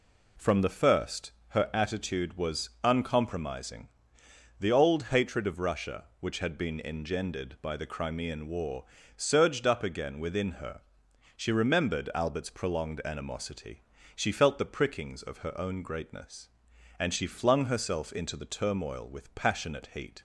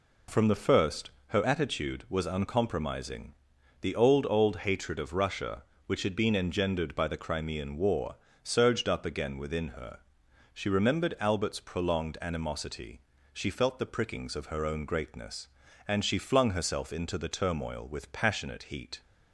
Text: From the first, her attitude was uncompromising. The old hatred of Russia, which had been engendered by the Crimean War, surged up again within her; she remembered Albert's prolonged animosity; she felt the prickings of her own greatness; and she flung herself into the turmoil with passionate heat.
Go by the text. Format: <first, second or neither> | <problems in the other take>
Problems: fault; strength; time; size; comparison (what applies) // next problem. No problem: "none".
first | says "old" twice; at 4.2 s